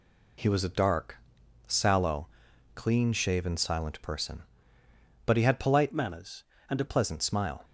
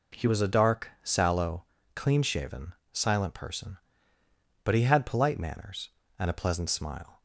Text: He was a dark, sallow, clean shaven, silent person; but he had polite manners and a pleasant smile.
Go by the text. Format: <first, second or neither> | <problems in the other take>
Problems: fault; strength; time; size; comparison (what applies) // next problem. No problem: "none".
second | changes voice from "manners" to "a"; from 5.9 to 6.8 s; 0.9 s long